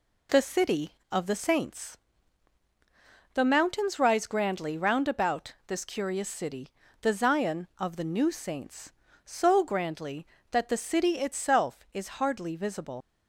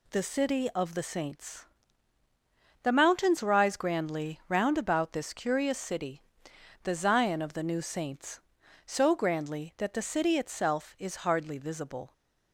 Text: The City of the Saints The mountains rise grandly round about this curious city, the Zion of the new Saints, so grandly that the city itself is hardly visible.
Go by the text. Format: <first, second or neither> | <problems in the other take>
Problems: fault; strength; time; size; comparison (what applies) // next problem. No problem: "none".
second | pauses between "Saints" and "The"; strong; at 1.9 s; 1.3 s long; also in the second // leaves "visible" unfinished; at 13.0 s; 80 ms